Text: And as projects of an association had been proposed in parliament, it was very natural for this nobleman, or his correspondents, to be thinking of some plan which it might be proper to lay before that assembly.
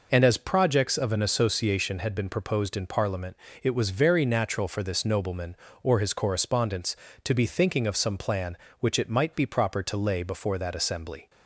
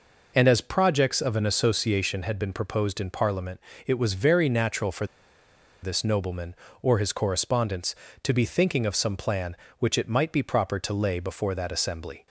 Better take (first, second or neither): first